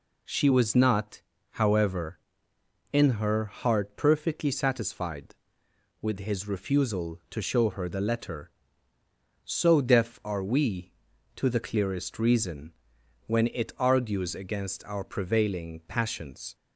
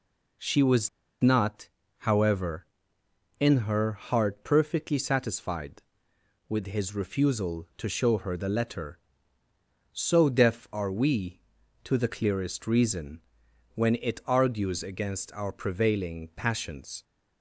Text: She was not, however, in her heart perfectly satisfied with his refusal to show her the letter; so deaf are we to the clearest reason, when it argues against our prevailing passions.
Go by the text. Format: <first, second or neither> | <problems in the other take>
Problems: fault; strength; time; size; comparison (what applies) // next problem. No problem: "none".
first | pauses between "was" and "not"; slight; at 0.8 s; 0.32 s long